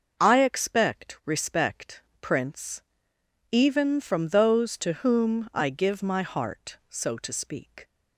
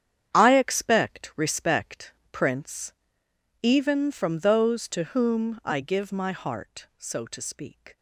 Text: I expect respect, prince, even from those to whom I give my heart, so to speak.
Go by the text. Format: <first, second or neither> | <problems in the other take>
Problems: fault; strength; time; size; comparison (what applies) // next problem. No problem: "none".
first | gets quieter; strong; throughout; 11 dB // starts louder than the rest; strong; until 1.3 s; 9 dB; noticeable in the first